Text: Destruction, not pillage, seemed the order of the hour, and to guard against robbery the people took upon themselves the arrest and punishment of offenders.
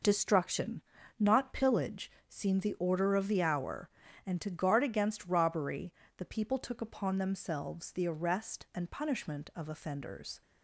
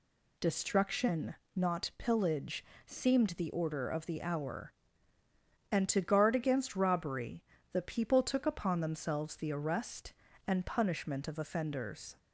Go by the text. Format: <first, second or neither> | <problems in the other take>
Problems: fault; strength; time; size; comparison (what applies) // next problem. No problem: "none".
neither | pauses between "robbery" and "the"; slight; the same in both